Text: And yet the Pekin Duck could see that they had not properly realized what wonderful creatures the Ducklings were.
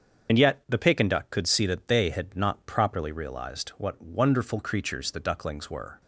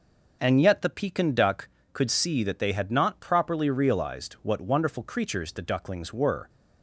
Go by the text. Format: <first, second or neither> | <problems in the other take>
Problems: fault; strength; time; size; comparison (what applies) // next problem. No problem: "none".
second | loses the start of "And"; at 0.2 s; 75 ms // starts louder than the rest; strong; until 1.3 s; 7 dB